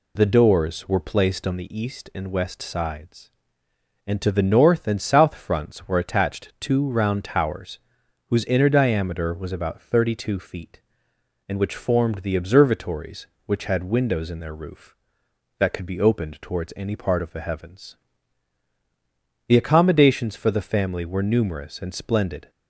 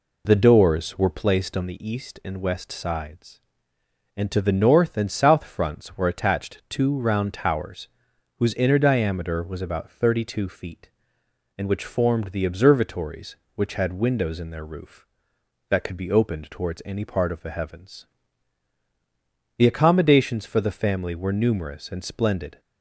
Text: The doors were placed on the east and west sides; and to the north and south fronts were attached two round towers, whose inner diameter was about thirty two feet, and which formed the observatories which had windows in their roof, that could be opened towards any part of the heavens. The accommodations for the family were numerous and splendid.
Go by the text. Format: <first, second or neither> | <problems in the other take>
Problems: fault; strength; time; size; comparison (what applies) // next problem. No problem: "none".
first | starts louder than the rest; slight; until 1.2 s; 3 dB